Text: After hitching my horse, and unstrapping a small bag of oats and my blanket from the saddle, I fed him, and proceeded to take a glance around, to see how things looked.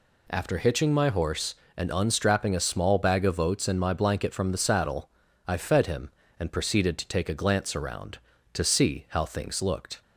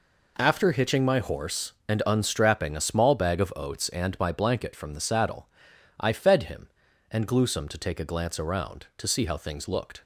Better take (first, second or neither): first